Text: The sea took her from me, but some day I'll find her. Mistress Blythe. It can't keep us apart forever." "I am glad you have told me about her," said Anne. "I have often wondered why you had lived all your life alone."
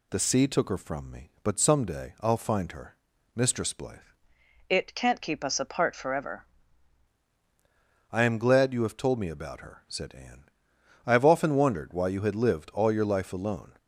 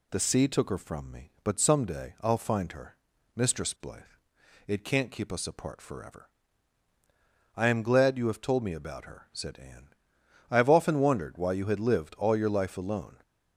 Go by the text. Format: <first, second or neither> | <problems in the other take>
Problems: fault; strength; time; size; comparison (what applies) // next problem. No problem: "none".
second | changes voice from "It" to "forever"; from 4.6 to 6.4 s; 1.8 s long